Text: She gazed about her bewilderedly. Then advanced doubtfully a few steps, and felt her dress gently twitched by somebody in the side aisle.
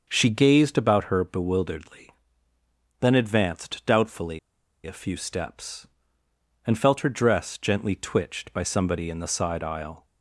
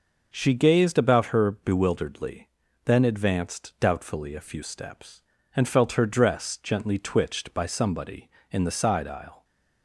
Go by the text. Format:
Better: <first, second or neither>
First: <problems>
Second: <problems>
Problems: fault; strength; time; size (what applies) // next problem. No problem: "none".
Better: second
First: starts louder than the rest; until 1.0 s; 6.5 dB // pauses between "doubtfully" and "a"; at 4.3 s; 0.45 s long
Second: none